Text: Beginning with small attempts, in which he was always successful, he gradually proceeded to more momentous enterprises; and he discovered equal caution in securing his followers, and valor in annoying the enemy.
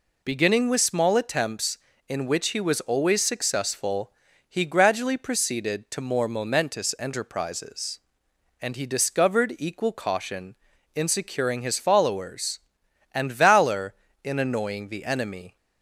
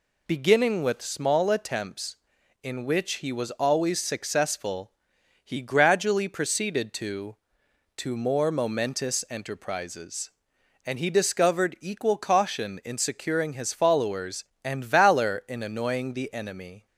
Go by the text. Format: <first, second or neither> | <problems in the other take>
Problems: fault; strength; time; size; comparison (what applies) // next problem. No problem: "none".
first | says "to" twice; at 7.9 s